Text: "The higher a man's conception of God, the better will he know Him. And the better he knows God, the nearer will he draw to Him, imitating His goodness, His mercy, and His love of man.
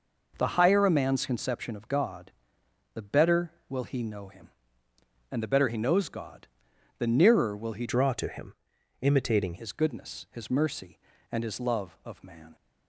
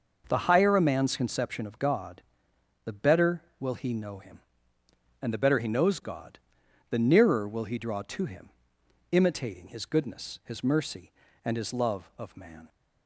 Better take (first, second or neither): second